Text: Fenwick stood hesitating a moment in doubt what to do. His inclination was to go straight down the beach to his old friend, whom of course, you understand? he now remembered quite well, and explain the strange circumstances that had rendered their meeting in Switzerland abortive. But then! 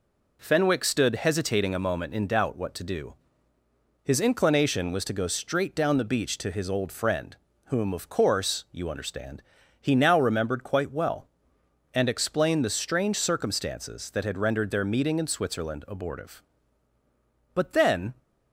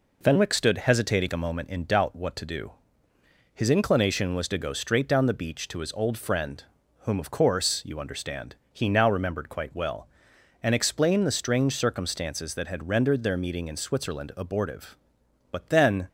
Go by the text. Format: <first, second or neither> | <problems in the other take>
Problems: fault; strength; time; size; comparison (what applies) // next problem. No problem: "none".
neither | none